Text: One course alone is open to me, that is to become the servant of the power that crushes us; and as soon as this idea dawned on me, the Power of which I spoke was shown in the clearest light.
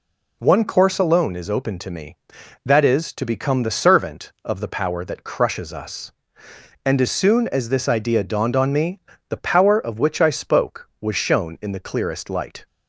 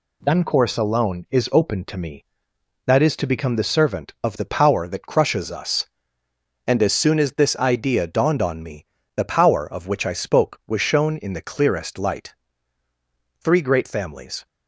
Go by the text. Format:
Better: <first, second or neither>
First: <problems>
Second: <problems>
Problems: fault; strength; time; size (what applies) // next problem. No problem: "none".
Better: first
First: none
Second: goes on to say "Three great families"; noticeable; from 13.4 s on; 1.0 s long